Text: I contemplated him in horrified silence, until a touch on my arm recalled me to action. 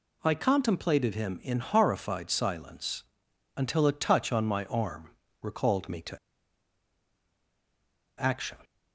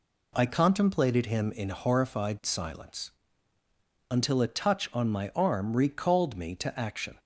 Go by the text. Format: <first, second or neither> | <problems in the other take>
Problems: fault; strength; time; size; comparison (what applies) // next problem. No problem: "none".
second | pauses between "arm" and "recalled"; slight; at 5.1 s; 0.30 s long // pauses between "to" and "action"; strong; at 6.1 s; 2.0 s long